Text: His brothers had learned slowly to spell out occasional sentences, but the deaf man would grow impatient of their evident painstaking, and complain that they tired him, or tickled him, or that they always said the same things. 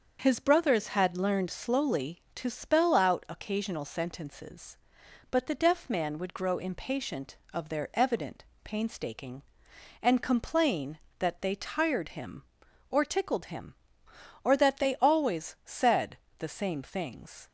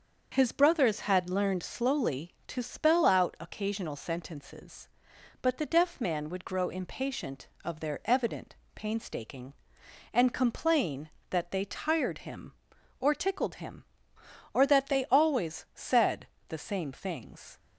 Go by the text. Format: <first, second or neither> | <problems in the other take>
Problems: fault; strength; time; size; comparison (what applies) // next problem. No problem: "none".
neither | starts louder than the rest; the same in both // pauses between "evident" and "painstaking"; slight; the same in both // pauses between "said" and "the"; slight; the same in both